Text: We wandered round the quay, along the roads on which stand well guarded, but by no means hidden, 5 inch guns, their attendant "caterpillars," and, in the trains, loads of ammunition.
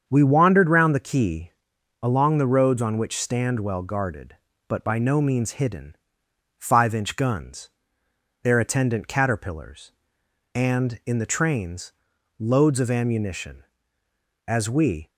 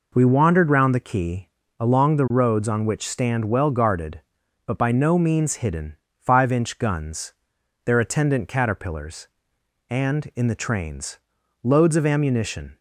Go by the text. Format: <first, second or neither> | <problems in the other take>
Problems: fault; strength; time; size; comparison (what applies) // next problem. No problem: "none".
second | starts louder than the rest; strong; until 1.0 s; 7 dB // goes on to say "As we"; noticeable; from 14.4 s on; 0.62 s long